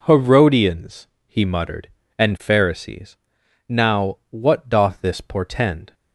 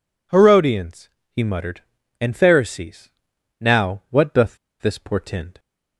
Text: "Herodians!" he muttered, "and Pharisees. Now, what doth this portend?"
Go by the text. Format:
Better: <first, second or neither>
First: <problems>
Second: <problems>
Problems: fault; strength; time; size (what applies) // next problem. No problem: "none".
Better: first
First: none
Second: pauses between "doth" and "this"; slight; at 4.5 s; 0.23 s long